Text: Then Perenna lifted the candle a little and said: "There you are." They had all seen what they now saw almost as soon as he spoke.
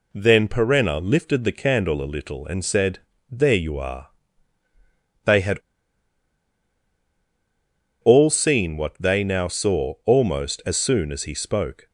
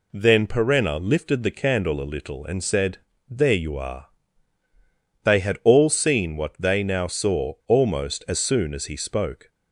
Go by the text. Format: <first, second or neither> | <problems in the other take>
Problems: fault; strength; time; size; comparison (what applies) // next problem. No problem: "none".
second | pauses between "had" and "all"; strong; at 5.5 s; 2.4 s long